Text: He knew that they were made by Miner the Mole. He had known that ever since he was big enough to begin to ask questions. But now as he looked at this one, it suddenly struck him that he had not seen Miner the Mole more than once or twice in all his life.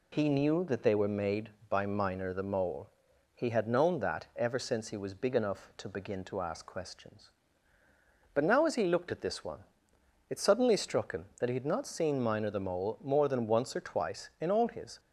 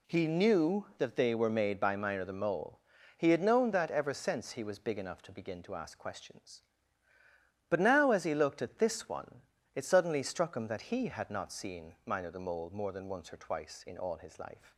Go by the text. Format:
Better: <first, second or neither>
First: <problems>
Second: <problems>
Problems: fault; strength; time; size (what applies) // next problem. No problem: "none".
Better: second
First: stops before "life"; at 14.9 s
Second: none